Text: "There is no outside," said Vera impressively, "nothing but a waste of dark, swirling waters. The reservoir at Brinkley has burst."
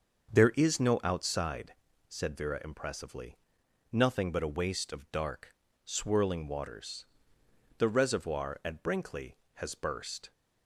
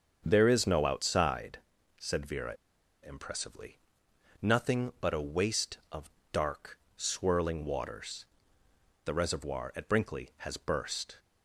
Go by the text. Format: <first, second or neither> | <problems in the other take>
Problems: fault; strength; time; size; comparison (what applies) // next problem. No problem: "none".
first | starts louder than the rest; until 1.2 s; 7 dB; also in the first // pauses between "Vera" and "impressively"; noticeable; at 2.5 s; 0.48 s long // pauses between "of" and "dark"; slight; at 6.1 s; 0.20 s long